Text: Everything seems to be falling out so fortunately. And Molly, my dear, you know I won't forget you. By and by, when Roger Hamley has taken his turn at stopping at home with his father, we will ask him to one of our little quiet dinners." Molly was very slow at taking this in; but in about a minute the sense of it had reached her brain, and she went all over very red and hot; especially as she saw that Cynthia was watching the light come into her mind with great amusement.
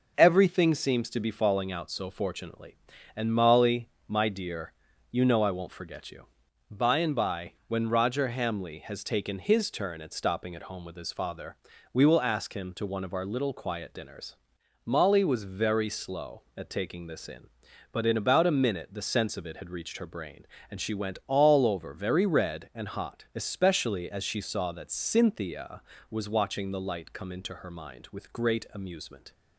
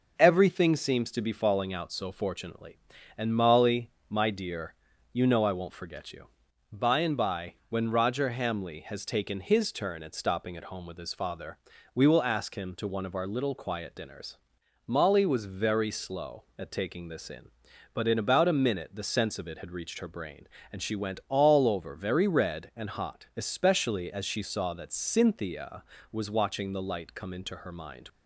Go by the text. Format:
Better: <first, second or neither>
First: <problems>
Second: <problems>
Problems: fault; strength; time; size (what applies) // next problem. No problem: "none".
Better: first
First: none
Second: stops before "with great amusement"; at 28.0 s